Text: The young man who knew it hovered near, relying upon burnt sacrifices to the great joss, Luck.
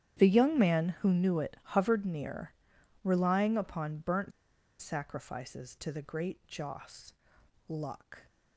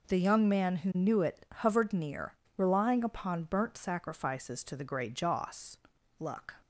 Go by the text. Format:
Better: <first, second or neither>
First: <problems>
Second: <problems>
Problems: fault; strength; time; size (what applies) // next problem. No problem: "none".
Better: second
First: starts louder than the rest; strong; until 1.2 s; 10 dB // pauses between "burnt" and "sacrifices"; noticeable; at 4.3 s; 0.50 s long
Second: none